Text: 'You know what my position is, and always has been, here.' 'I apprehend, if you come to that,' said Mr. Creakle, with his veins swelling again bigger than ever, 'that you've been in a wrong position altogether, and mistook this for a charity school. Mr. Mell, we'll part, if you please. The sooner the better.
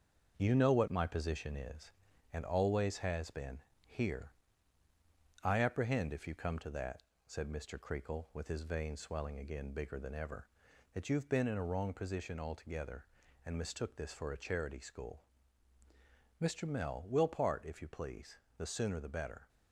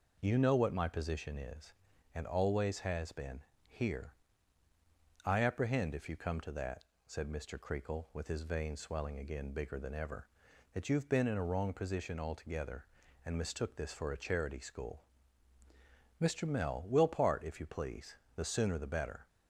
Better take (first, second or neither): second